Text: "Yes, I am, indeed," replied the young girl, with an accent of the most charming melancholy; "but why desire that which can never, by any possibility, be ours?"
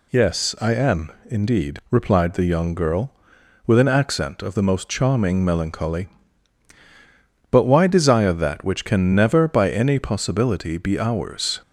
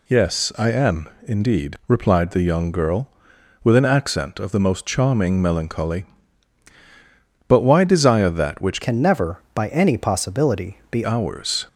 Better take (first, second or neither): first